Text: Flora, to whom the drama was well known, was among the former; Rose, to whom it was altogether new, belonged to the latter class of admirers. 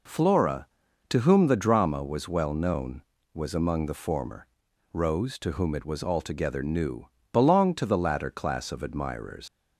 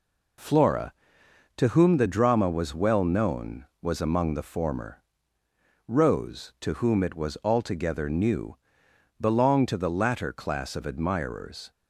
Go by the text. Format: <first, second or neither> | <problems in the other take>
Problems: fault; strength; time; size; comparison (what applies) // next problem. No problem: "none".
second | leaves "admirers" unfinished; at 9.4 s; 85 ms